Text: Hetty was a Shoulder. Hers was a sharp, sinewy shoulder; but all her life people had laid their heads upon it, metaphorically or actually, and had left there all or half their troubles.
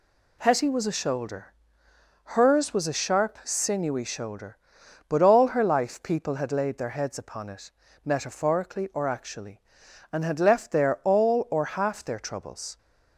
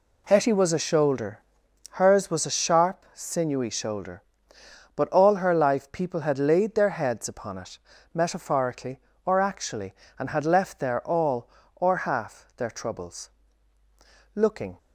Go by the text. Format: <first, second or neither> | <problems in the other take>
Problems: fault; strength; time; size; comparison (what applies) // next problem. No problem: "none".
first | goes on to say "Looking"; slight; from 14.3 s on; 0.44 s long